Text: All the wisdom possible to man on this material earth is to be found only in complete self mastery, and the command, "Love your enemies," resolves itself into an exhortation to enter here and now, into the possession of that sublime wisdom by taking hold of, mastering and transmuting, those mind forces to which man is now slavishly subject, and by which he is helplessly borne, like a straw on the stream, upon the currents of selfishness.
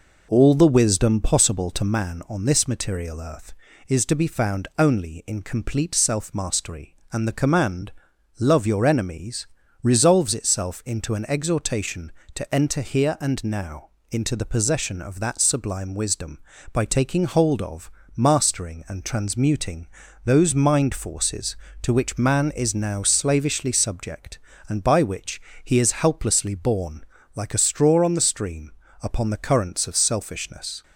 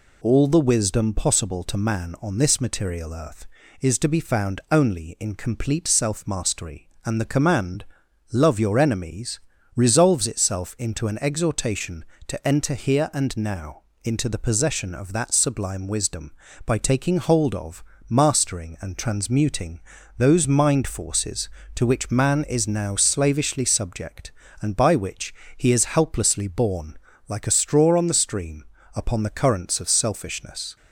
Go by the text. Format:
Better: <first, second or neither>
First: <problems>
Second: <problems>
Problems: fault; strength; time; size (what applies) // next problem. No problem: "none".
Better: second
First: starts louder than the rest; noticeable; until 1.9 s; 5 dB // pauses between "which" and "he"; slight; at 25.4 s; 0.24 s long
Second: pauses between "which" and "he"; slight; at 25.3 s; 0.24 s long